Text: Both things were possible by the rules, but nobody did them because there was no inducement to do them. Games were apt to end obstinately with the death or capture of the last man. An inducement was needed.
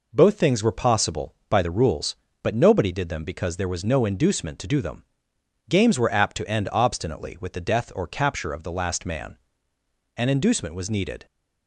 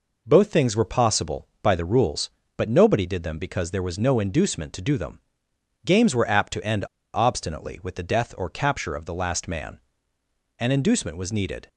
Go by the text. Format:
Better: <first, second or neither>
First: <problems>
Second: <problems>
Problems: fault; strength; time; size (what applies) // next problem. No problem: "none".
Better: first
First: none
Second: pauses between "end" and "obstinately"; slight; at 6.8 s; 0.28 s long